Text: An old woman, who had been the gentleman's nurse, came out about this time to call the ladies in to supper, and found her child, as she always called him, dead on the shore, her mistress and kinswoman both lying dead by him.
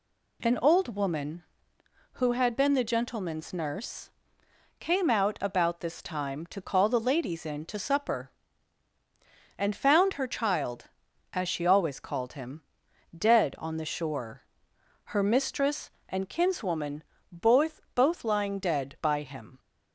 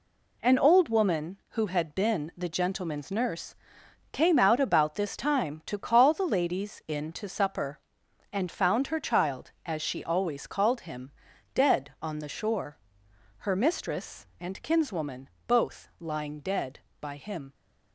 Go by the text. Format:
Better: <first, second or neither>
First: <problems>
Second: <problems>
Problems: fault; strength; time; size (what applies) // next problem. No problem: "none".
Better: second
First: pauses between "kinswoman" and "both"; slight; at 17.0 s; 0.28 s long // says "both" twice; at 17.9 s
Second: pauses between "kinswoman" and "both"; slight; at 15.2 s; 0.20 s long